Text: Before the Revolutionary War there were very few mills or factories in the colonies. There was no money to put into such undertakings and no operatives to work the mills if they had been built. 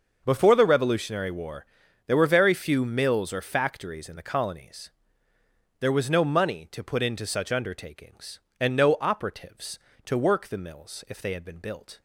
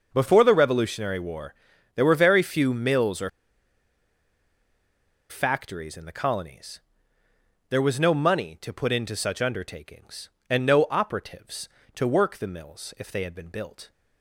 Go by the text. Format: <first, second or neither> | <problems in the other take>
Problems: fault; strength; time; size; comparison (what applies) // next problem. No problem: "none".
first | starts louder than the rest; until 1.1 s; 6 dB; also in the first // pauses between "War" and "there"; at 1.5 s; 0.42 s long; also in the first // pauses between "or" and "factories"; strong; at 3.2 s; 2.0 s long